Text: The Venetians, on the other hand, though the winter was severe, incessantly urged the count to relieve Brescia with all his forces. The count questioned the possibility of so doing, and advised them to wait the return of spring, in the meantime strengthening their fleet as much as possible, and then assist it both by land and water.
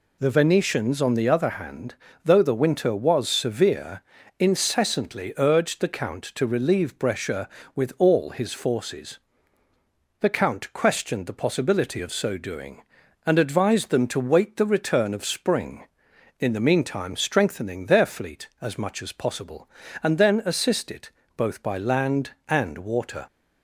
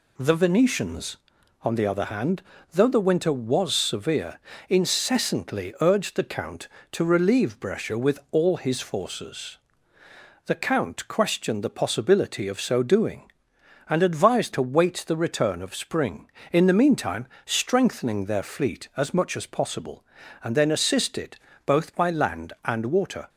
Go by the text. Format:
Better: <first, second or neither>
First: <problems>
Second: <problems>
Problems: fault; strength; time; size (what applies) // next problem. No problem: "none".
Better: first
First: pauses between "it" and "both"; slight; at 21.1 s; 0.26 s long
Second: skips "them"; at 14.5 s // pauses between "meantime" and "strengthening"; slight; at 17.2 s; 0.16 s long // pauses between "it" and "both"; slight; at 21.3 s; 0.28 s long